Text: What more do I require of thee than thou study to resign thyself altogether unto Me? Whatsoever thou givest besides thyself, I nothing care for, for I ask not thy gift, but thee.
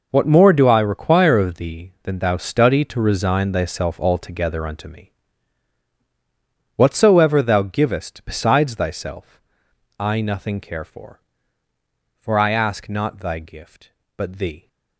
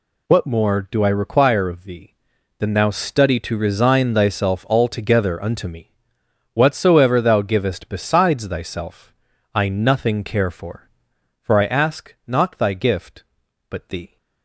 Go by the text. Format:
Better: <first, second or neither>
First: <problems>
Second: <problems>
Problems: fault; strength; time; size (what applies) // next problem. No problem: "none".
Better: neither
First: none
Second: none